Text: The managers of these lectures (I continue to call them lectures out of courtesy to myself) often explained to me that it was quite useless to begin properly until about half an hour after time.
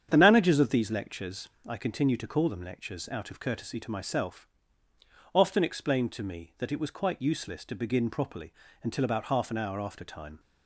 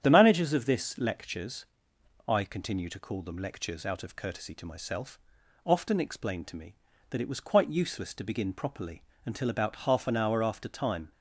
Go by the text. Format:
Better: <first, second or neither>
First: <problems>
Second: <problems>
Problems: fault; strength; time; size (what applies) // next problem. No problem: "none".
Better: first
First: starts louder than the rest; strong; until 1.1 s; 8.5 dB // pauses between "properly" and "until"; slight; at 8.5 s; 0.30 s long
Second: starts louder than the rest; strong; until 1.0 s; 9 dB // says "this" for "these"; at 0.6 s // pauses between "properly" and "until"; slight; at 9.0 s; 0.24 s long